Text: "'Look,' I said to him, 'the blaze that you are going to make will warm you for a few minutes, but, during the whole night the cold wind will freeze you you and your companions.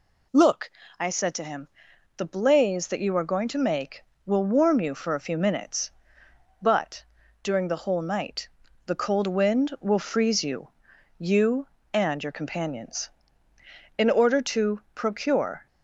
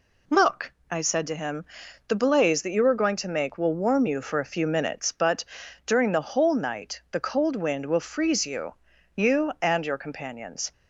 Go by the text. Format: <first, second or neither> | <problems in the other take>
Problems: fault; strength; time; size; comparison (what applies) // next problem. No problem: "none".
second | pauses between "night" and "the"; at 8.4 s; 0.38 s long // pauses between "you" and "you"; noticeable; at 10.6 s; 0.52 s long; also in the second // goes on to say "In order to procure"; strong; from 13.9 s on; 1.6 s long